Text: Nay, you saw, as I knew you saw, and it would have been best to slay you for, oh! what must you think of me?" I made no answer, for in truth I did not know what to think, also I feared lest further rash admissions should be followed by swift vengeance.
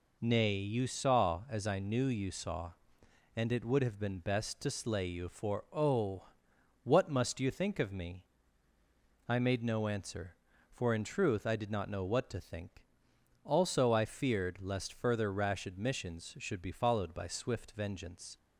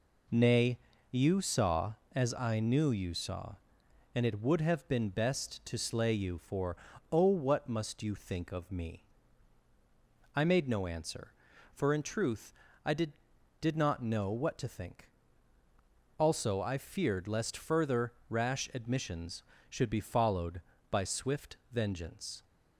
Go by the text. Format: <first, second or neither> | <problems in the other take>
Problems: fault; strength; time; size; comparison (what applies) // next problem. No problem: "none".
first | pauses between "truth" and "I"; slight; at 12.5 s; 0.32 s long // says "did" twice; at 13.6 s // pauses between "further" and "rash"; slight; at 18.1 s; 0.18 s long // pauses between "swift" and "vengeance"; slight; at 21.5 s; 0.16 s long